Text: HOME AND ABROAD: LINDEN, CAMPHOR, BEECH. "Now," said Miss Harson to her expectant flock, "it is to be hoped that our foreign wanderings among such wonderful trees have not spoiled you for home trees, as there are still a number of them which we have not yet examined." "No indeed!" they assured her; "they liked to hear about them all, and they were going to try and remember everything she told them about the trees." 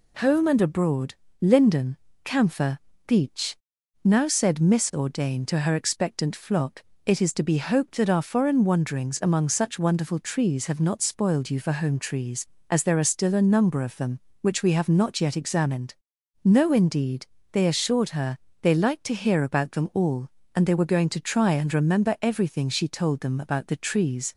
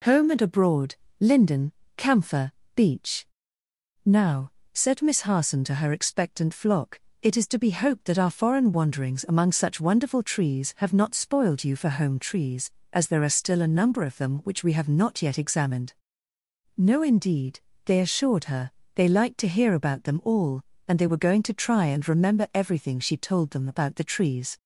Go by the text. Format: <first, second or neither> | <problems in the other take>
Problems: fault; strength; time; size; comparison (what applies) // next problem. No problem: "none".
second | says "Ordain" for "Harson"; at 4.9 s